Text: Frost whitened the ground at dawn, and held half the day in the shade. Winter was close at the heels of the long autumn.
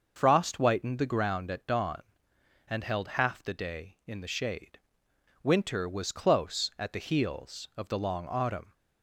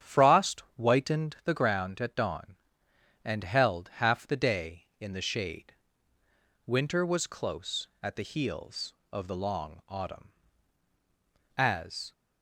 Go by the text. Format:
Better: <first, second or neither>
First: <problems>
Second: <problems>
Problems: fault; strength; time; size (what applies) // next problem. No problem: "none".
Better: first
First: starts louder than the rest; until 1.1 s; 6 dB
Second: starts louder than the rest; strong; until 1.1 s; 8.5 dB // goes on to say "As"; from 11.5 s on; 0.56 s long